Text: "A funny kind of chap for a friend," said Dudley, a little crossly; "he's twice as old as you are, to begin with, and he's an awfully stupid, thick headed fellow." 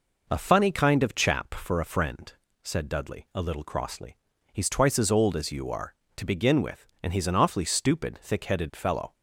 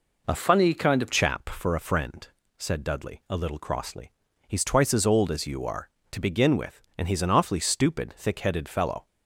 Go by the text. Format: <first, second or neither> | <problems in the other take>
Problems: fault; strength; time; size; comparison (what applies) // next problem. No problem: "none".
first | changes voice from "funny" to "of"; from 0.3 to 1.1 s; 0.8 s long